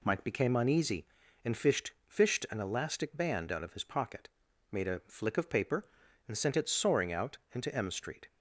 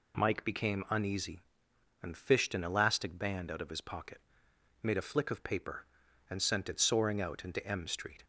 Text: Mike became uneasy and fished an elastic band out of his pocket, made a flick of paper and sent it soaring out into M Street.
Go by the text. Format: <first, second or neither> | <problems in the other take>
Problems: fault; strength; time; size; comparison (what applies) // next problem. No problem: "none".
second | says "fished" twice; at 2.0 s // pauses between "out" and "into"; slight; at 7.3 s; 0.16 s long